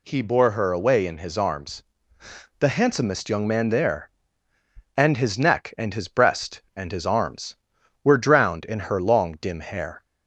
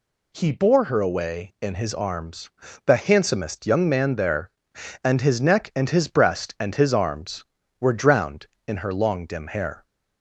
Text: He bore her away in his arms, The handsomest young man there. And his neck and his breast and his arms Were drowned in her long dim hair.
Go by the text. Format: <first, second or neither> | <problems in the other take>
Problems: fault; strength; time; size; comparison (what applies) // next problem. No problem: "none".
neither | none